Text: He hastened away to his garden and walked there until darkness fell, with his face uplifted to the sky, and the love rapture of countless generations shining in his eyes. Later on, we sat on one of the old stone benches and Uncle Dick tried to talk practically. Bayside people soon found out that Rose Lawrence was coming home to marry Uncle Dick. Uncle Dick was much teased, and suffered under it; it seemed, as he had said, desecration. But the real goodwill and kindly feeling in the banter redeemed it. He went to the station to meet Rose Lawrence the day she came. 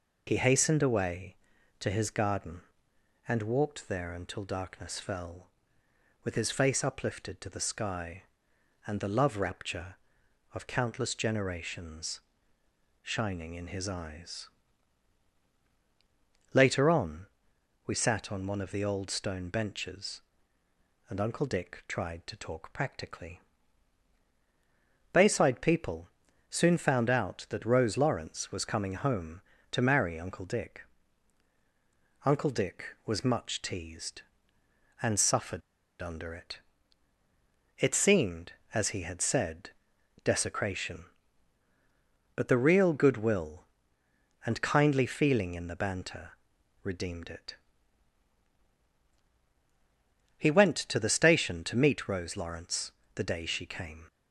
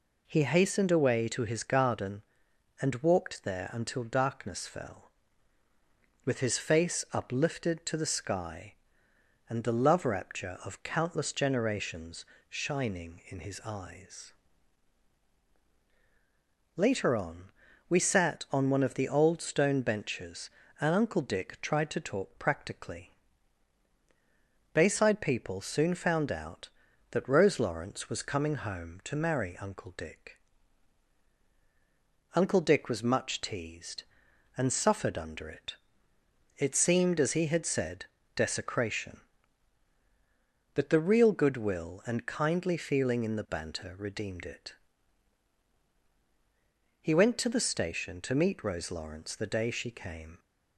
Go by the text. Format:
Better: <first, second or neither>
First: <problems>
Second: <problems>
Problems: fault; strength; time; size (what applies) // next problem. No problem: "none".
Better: second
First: pauses between "generations" and "shining"; noticeable; at 12.2 s; 0.82 s long // pauses between "people" and "soon"; at 26.0 s; 0.42 s long // pauses between "suffered" and "under"; at 35.6 s; 0.39 s long // pauses between "banter" and "redeemed"; noticeable; at 46.3 s; 0.54 s long // pauses between "Lawrence" and "the"; slight; at 52.9 s; 0.22 s long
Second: pauses between "generations" and "shining"; slight; at 12.2 s; 0.26 s long